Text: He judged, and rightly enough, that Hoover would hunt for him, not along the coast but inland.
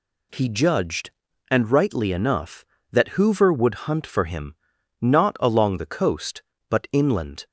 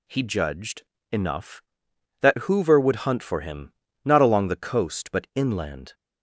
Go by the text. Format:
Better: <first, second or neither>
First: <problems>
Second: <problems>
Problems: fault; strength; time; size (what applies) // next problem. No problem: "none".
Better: first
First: none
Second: skips "and rightly"; at 0.9 s